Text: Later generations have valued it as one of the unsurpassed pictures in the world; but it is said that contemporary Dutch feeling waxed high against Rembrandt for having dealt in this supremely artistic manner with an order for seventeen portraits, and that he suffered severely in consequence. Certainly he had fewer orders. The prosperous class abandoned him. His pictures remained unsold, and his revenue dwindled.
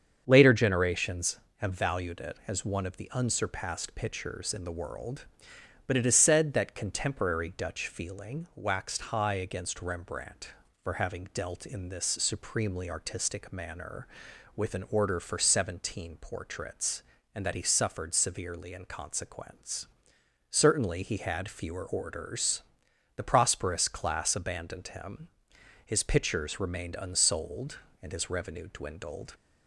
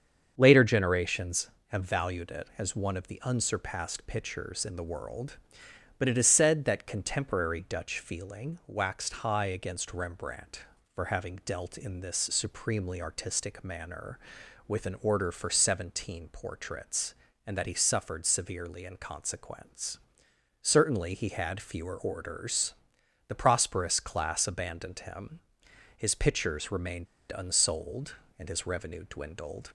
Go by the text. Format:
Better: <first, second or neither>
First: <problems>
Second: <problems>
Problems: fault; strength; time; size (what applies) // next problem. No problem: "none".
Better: first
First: starts louder than the rest; strong; until 1.2 s; 7.5 dB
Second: starts louder than the rest; strong; until 1.3 s; 7.5 dB // pauses between "remained" and "unsold"; slight; at 27.0 s; 0.26 s long